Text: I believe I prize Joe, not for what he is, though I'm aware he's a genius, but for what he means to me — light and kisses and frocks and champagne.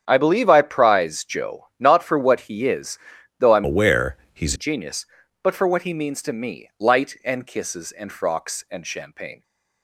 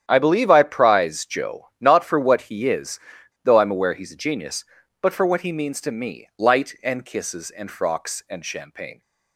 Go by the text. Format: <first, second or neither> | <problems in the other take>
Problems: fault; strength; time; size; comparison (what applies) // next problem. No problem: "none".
second | starts louder than the rest; strong; until 1.0 s; 8.5 dB; strong in the second // changes voice from "aware" to "he's"; from 3.6 to 4.5 s; 0.9 s long // pauses between "aware" and "he's"; slight; at 4.1 s; 0.18 s long